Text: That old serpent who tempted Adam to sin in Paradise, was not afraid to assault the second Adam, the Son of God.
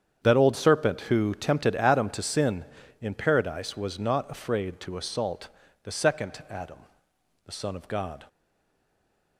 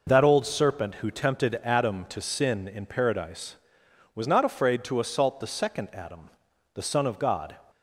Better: second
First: starts louder than the rest; strong; until 1.2 s; 8 dB // pauses between "assault" and "the"; slight; at 5.4 s; 0.34 s long // stays silent after the last word; from 8.2 s on; 1.1 s long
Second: none

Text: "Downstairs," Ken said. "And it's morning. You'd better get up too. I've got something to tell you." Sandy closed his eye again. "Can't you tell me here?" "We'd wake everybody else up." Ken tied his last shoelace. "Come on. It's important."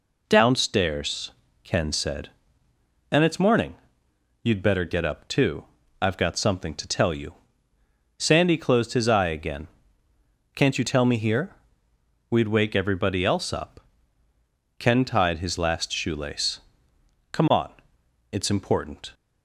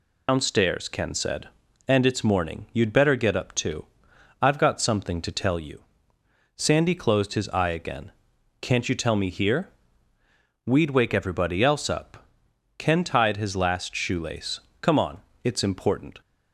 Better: first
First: none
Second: loses the start of "Downstairs"; at 0.2 s; 145 ms

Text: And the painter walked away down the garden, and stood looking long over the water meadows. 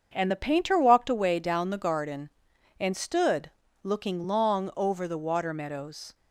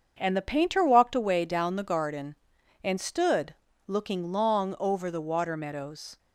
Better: neither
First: starts louder than the rest; until 1.1 s; 7 dB // pauses between "stood" and "looking"; slight; at 3.4 s; 0.32 s long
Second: starts louder than the rest; until 1.2 s; 7 dB // pauses between "stood" and "looking"; slight; at 3.5 s; 0.32 s long

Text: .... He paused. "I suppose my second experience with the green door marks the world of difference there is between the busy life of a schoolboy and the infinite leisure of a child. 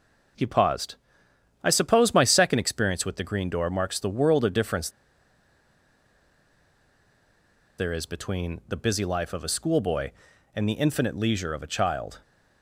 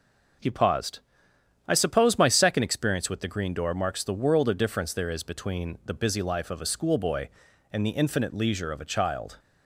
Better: second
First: starts louder than the rest; noticeable; until 2.0 s; 6 dB // pauses between "difference" and "there"; strong; at 4.8 s; 2.8 s long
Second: starts louder than the rest; noticeable; until 2.0 s; 6 dB

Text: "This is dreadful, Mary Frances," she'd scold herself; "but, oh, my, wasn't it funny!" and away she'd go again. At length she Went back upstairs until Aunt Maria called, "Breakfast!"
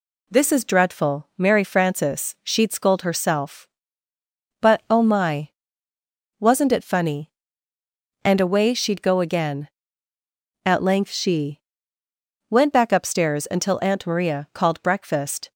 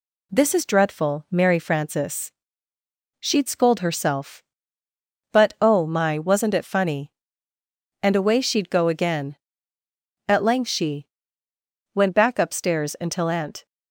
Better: first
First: pauses between "she" and "Went"; noticeable; at 11.6 s; 0.88 s long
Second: pauses between "she" and "Went"; noticeable; at 11.0 s; 0.88 s long // stops before "Maria called Breakfast"; at 13.6 s

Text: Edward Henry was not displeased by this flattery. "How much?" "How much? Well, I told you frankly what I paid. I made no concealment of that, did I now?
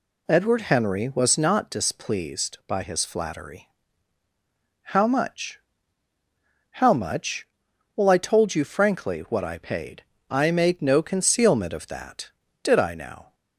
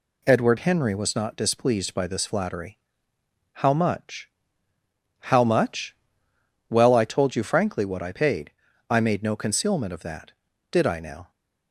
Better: second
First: says "his" for "this"; at 2.8 s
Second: none

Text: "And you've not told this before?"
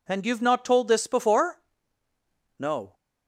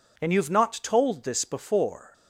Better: second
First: goes on to say "No"; slight; from 2.6 s on; 0.34 s long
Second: none

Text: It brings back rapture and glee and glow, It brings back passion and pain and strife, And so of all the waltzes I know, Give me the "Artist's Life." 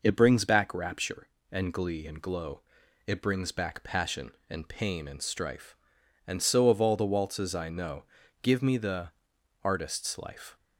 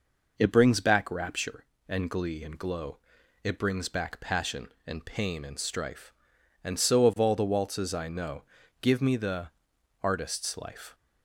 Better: neither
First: pauses between "the" and "Artist's"; noticeable; at 9.0 s; 0.52 s long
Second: pauses between "the" and "Artist's"; noticeable; at 9.4 s; 0.52 s long

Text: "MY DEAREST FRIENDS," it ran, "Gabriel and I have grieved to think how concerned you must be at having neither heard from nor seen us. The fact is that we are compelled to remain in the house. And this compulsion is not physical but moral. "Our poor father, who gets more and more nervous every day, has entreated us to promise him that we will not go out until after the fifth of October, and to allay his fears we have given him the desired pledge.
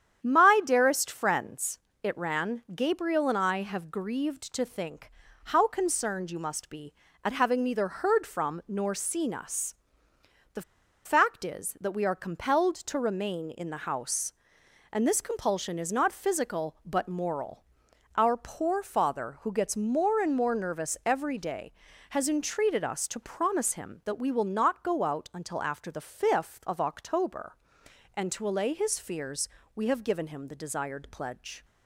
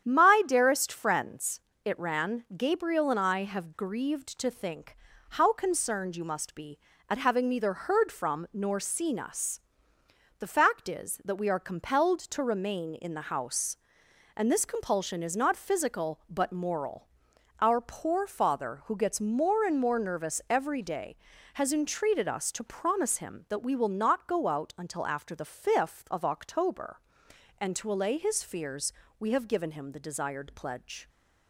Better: second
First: starts louder than the rest; strong; until 1.2 s; 9 dB // pauses between "think" and "how"; slight; at 5.0 s; 0.36 s long // pauses between "The" and "fact"; at 10.6 s; 0.43 s long // pauses between "fears" and "we"; slight; at 29.4 s; 0.26 s long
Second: starts louder than the rest; strong; until 1.0 s; 9 dB // pauses between "think" and "how"; slight; at 4.9 s; 0.36 s long // pauses between "fears" and "we"; slight; at 28.9 s; 0.26 s long

